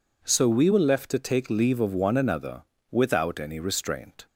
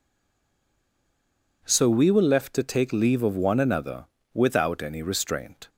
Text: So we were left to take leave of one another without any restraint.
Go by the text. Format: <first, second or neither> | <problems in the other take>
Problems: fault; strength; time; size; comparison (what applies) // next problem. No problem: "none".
first | stays silent before the first word; noticeable; until 1.6 s; 1.6 s long // pauses between "another" and "without"; slight; at 4.0 s; 0.28 s long; slight in the first